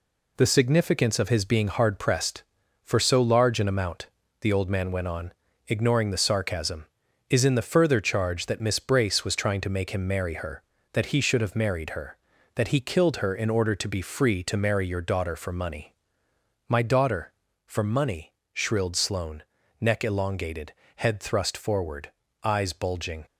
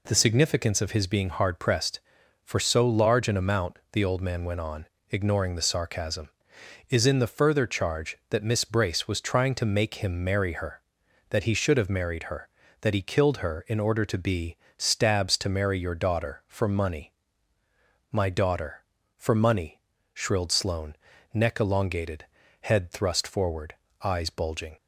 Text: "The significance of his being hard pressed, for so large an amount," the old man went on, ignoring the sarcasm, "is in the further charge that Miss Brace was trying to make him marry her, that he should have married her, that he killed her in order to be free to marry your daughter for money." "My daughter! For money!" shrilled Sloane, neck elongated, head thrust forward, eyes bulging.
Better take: first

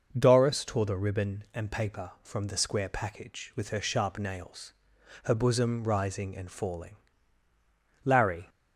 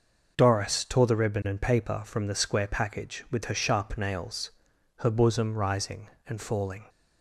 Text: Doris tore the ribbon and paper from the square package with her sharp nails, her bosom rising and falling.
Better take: second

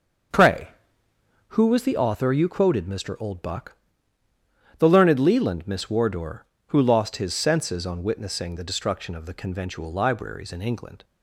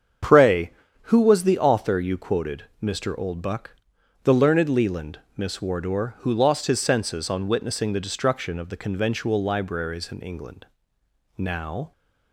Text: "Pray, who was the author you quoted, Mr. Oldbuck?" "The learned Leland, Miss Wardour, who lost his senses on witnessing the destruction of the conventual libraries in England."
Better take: first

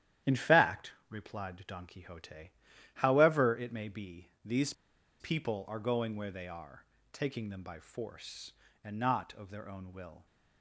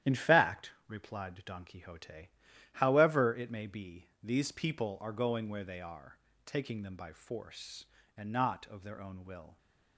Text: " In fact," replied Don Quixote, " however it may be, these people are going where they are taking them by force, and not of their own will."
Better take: second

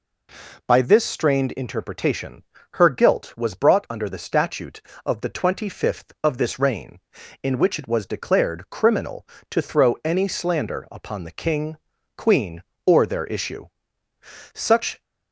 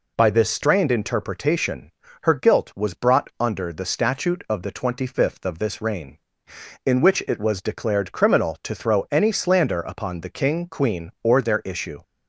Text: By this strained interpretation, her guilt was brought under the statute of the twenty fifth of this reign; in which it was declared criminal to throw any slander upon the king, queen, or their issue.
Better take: second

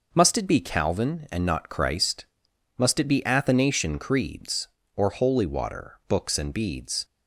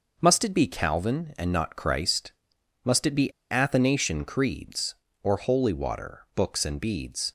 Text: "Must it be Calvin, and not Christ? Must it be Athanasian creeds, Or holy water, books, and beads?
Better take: first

